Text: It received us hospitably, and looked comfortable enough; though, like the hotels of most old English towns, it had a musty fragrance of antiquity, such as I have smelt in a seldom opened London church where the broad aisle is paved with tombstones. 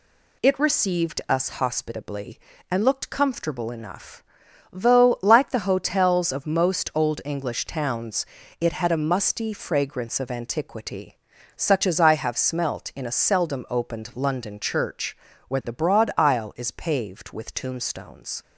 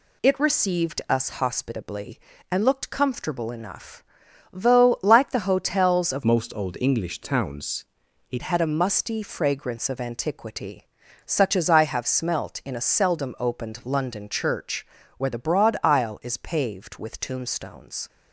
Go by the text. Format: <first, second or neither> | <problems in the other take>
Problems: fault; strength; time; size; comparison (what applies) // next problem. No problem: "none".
first | changes voice from "most" to "it"; from 6.2 to 8.4 s; 2.2 s long // pauses between "church" and "where"; slight; at 14.8 s; 0.32 s long; slight in the first